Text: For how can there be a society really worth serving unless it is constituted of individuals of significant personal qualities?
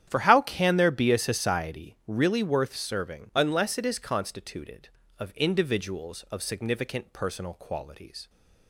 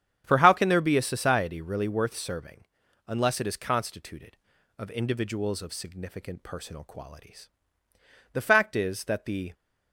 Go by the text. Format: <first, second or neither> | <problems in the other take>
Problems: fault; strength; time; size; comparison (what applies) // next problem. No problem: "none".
first | starts louder than the rest; strong; until 1.2 s; 8.5 dB; strong in the first // pauses between "serving" and "unless"; at 2.6 s; 0.42 s long // goes on to say "The fact is that the"; noticeable; from 8.3 s on; 1.2 s long